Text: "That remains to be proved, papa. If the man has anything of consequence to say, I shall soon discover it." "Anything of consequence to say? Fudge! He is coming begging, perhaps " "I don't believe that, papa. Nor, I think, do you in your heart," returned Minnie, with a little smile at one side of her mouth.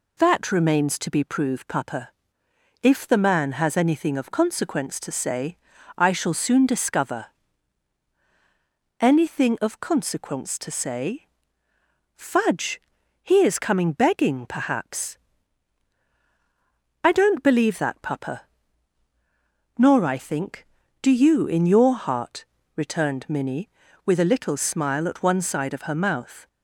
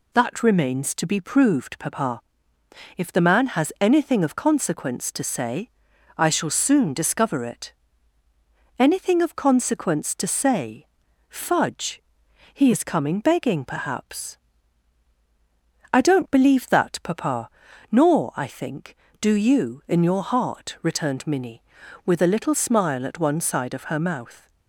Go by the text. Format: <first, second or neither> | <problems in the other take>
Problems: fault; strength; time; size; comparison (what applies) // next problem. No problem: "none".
second | skips "it"; at 8.1 s